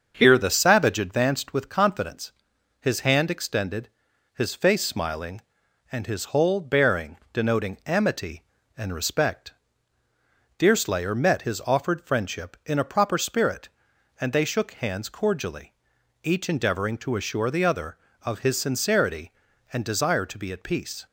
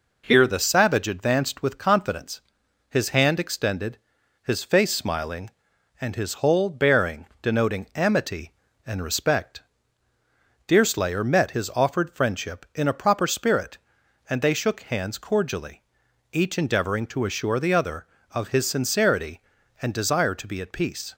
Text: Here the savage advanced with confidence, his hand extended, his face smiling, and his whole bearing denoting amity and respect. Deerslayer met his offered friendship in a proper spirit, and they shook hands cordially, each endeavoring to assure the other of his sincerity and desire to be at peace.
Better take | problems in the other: second | starts louder than the rest; until 1.3 s; 7 dB // pauses between "bearing" and "denoting"; slight; at 7.1 s; 0.16 s long; slight in the second

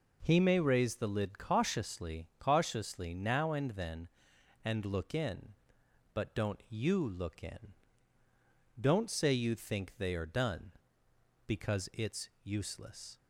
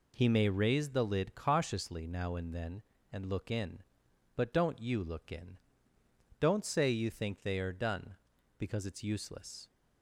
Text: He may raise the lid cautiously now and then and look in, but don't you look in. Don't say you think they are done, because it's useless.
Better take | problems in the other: second | says "cautiously" twice; at 2.3 s

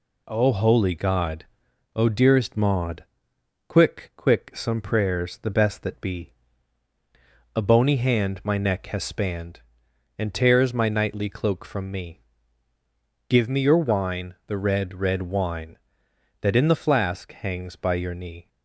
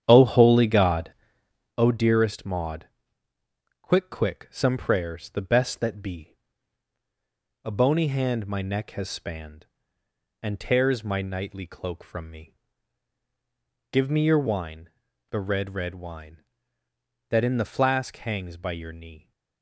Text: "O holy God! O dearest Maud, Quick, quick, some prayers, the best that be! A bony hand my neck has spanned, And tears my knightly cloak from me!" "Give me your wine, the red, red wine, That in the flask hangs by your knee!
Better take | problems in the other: first | starts louder than the rest; strong; until 1.8 s; 9.5 dB

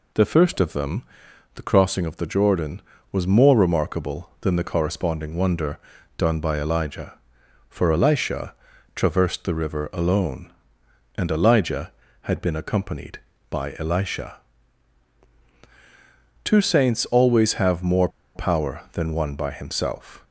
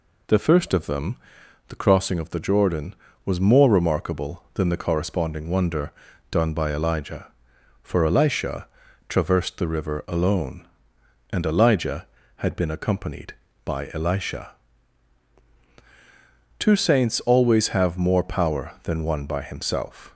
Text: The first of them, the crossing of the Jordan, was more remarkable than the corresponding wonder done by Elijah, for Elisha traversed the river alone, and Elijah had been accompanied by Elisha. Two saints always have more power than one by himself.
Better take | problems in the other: second | pauses between "wonder" and "done"; at 5.7 s; 0.40 s long; also in the second // pauses between "Elisha" and "traversed"; at 8.5 s; 0.40 s long; also in the second // pauses between "more" and "power"; slight; at 18.0 s; 0.27 s long

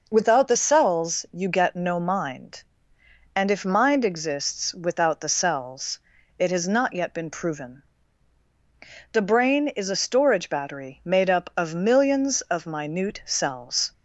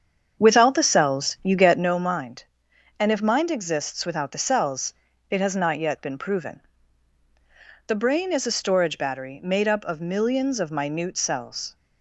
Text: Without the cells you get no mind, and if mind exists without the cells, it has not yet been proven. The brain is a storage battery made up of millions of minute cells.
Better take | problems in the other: first | starts louder than the rest; strong; until 1.9 s; 7 dB

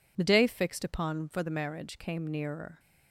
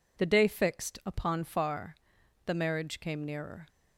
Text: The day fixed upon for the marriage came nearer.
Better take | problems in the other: first | says "far" for "for"; at 1.4 s

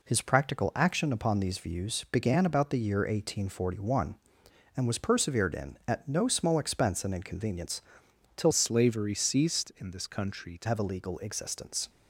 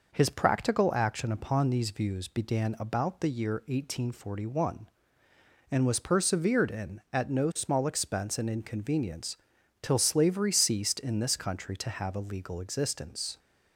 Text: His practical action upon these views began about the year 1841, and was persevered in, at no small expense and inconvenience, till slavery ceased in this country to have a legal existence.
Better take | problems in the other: second | changes voice from "slavery" to "to"; from 8.5 to 10.6 s; 2.1 s long

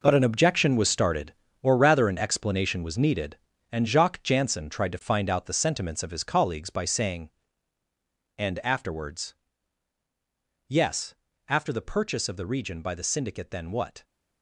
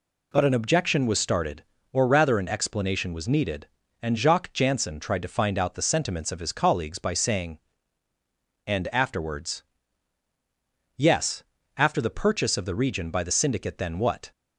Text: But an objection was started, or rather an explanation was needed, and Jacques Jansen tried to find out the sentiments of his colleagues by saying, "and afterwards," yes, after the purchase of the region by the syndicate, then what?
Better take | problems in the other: second | gets quieter; strong; throughout; 11.5 dB

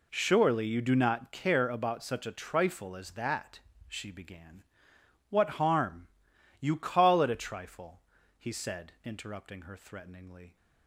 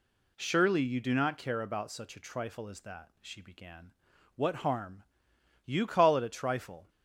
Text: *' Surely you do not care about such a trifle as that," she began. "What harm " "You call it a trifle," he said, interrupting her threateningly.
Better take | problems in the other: first | stops before "he said interrupting her threateningly"; at 6.8 s

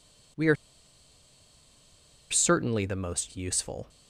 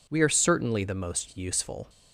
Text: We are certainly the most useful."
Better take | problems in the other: second | pauses between "are" and "certainly"; strong; at 0.5 s; 1.7 s long

